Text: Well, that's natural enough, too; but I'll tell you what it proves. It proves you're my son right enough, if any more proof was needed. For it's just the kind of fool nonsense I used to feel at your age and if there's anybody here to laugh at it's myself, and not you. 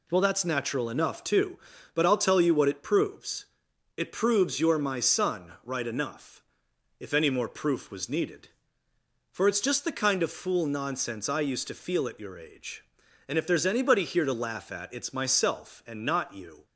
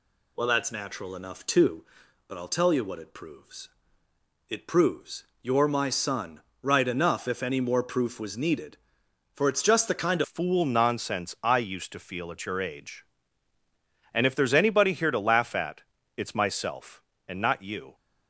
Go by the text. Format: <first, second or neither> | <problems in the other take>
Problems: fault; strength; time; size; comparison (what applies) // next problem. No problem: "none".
first | pauses between "proves" and "you're"; slight; at 5.2 s; 0.18 s long // pauses between "son" and "right"; slight; at 6.3 s; 0.22 s long // changes voice at "fool"; from 10.2 s on; 7.7 s long // pauses between "at" and "it's"; slight; at 15.8 s; 0.34 s long